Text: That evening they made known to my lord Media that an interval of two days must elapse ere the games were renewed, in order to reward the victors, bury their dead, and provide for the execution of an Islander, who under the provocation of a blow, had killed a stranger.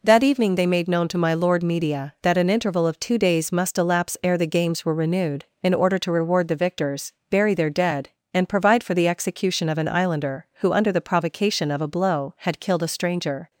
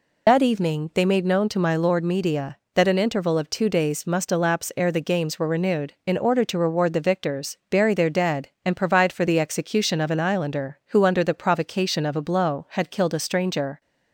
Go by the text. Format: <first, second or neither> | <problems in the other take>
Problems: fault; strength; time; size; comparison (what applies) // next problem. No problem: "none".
first | loses the start of "That"; at 0.2 s; 90 ms